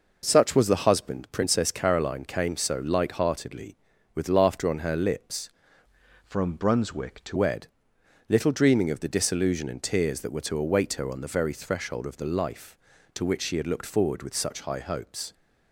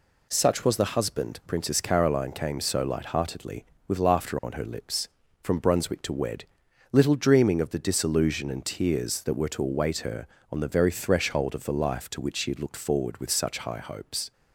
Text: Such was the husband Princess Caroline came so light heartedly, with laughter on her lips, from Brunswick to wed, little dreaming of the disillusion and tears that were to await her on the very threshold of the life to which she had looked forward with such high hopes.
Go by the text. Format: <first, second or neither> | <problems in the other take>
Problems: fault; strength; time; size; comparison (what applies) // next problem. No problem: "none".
second | changes voice from "from" to "to"; from 6.2 to 7.3 s; 1.1 s long